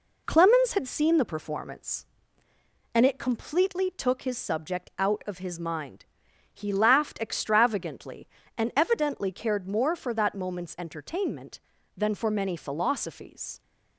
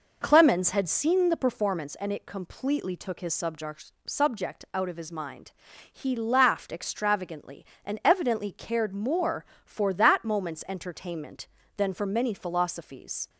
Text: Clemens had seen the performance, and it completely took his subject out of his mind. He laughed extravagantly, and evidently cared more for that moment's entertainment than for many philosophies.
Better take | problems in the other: first | says "subject" twice; at 4.0 s

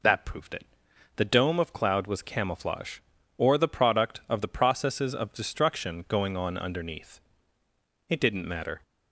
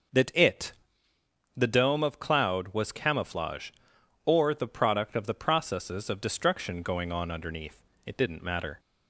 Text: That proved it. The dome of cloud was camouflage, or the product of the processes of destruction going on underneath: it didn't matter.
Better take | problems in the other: first | skips "proved"; at 0.3 s

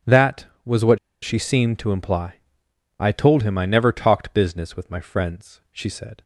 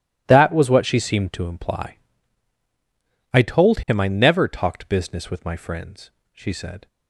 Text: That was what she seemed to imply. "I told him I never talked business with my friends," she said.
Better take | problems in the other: second | starts louder than the rest; strong; until 1.4 s; 8.5 dB // pauses between "what" and "she"; slight; at 0.9 s; 0.23 s long

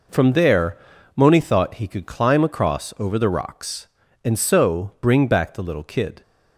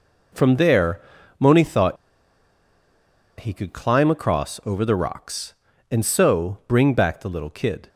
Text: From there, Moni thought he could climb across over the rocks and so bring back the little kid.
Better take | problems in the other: first | pauses between "thought" and "he"; strong; at 1.9 s; 1.4 s long

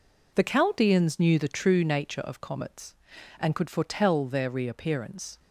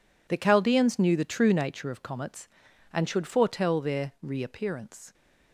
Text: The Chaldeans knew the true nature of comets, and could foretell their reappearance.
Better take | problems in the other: first | says "should" for "could"; at 3.0 s

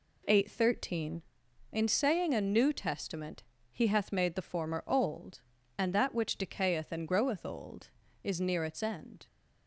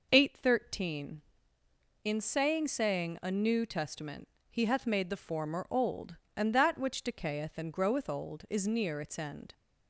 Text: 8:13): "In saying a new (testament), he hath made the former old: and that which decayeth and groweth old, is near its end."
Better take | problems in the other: first | says "saying" twice; at 2.6 s

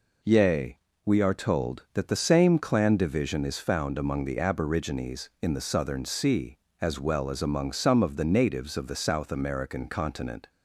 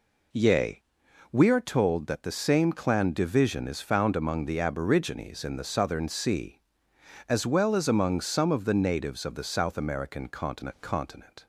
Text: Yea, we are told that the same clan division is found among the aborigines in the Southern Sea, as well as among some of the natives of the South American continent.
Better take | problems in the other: first | says "continent" twice; at 10.8 s

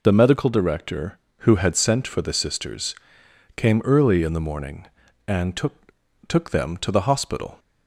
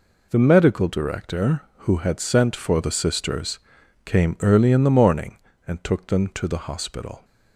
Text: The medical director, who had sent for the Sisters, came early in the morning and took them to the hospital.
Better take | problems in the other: second | says "took" twice; at 6.2 s

